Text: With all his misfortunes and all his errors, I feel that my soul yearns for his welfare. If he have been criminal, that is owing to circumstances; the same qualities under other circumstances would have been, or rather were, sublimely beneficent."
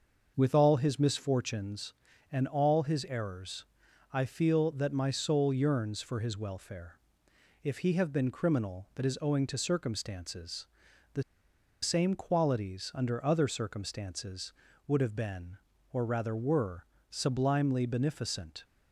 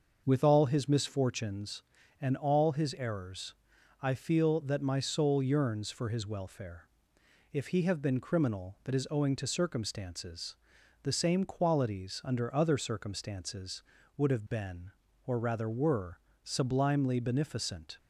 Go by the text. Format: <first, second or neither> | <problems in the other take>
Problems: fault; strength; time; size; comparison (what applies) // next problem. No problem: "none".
second | starts louder than the rest; until 1.3 s; 6 dB; also in the second // pauses between "the" and "same"; noticeable; at 11.2 s; 0.60 s long